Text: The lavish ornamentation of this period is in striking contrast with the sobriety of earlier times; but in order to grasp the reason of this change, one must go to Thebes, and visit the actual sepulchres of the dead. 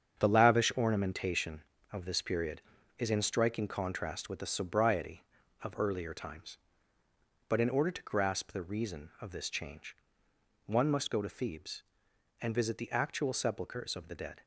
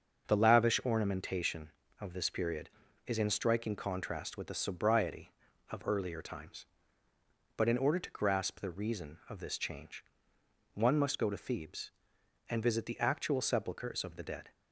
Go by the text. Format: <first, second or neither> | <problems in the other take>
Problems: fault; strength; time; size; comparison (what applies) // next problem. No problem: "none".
second | gets quieter; strong; throughout; 8 dB // starts louder than the rest; strong; until 1.2 s; 7.5 dB; also in the second